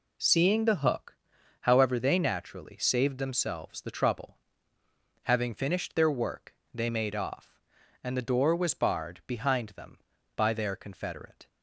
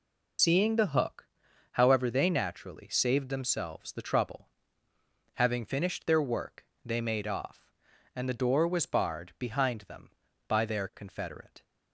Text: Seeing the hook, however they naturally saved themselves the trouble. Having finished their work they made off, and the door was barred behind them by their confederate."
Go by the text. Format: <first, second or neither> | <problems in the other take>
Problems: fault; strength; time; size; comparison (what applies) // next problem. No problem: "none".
first | loses the start of "Seeing"; at 0.3 s; 105 ms // pauses between "work" and "they"; slight; at 6.6 s; 0.20 s long; slight in the first